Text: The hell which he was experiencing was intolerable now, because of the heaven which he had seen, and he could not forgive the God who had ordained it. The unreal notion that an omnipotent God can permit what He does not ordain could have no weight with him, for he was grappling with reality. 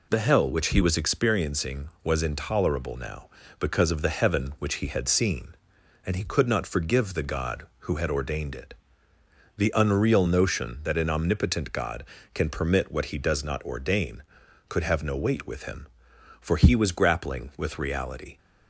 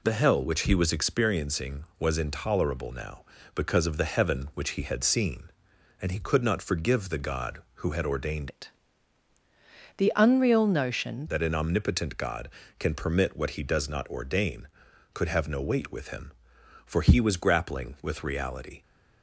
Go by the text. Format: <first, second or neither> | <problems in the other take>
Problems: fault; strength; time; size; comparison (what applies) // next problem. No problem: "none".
first | changes voice from "it" to "notion"; from 8.4 to 11.2 s; 2.8 s long